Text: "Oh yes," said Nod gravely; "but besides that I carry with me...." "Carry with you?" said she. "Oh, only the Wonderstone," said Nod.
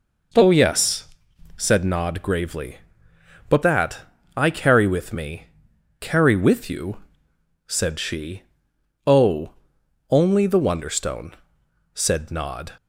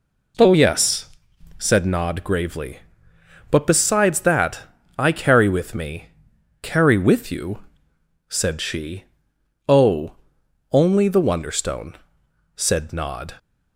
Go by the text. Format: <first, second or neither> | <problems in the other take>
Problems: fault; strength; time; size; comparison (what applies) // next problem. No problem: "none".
second | skips "besides"; at 3.6 s // pauses between "that" and "I"; slight; at 4.0 s; 0.34 s long; slight in the second